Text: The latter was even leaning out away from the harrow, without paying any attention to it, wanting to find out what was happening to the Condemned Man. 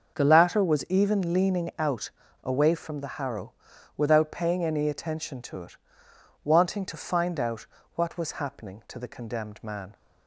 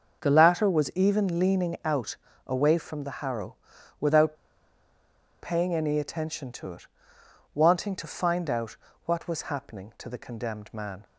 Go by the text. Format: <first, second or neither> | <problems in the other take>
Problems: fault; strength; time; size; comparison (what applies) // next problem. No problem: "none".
first | starts louder than the rest; until 1.2 s; 6.5 dB; also in the first // pauses between "out" and "away"; slight; at 2.1 s; 0.28 s long; slight in the first // pauses between "without" and "paying"; at 4.3 s; 1.0 s long // pauses between "out" and "what"; slight; at 8.7 s; 0.30 s long; slight in the first